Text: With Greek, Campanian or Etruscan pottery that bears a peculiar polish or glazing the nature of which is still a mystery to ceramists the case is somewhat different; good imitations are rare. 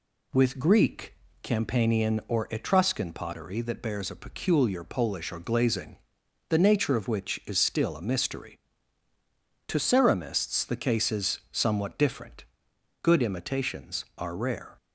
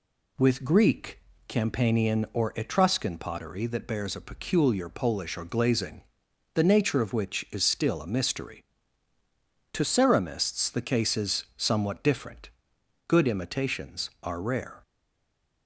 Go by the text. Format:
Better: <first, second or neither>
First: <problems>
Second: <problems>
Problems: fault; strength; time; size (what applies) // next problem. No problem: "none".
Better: first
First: pauses between "glazing" and "the"; noticeable; at 5.9 s; 0.54 s long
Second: pauses between "glazing" and "the"; noticeable; at 6.0 s; 0.54 s long // stays silent after the last word; slight; from 14.8 s on; 0.8 s long